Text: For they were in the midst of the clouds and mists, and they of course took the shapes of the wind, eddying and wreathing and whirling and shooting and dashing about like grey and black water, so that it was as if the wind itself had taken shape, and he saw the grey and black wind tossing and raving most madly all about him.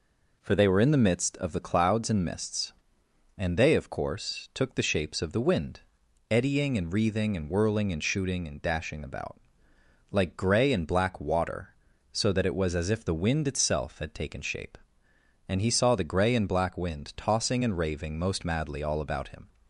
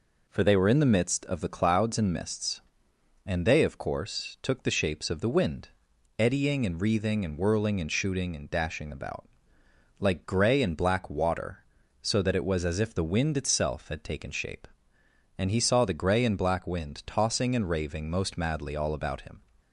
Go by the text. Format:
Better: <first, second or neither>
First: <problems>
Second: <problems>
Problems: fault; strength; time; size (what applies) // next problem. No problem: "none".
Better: neither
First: pauses between "about" and "like"; noticeable; at 9.3 s; 0.72 s long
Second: pauses between "about" and "like"; noticeable; at 9.2 s; 0.72 s long